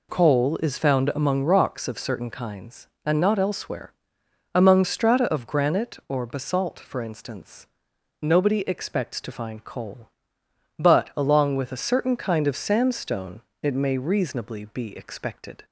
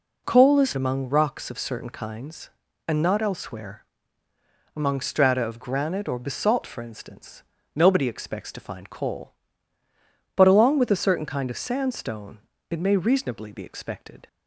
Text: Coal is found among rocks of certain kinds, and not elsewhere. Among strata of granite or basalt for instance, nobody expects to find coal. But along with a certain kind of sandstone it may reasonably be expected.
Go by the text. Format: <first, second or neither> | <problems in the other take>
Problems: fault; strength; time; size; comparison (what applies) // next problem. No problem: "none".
first | skips "found"; at 0.7 s // pauses between "sandstone" and "it"; slight; at 12.3 s; 0.32 s long; slight in the first